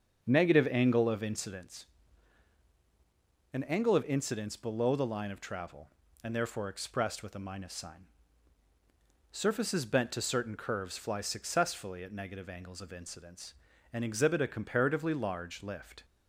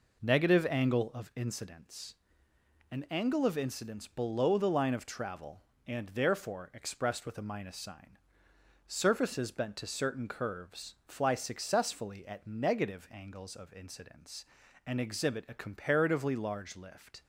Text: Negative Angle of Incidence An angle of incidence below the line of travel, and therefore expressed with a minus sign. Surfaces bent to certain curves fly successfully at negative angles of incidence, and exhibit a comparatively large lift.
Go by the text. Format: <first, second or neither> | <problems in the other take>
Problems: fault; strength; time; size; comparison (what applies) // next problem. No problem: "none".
second | starts louder than the rest; strong; until 1.7 s; 7 dB // pauses between "Incidence" and "An"; strong; at 1.8 s; 1.6 s long; noticeable in the second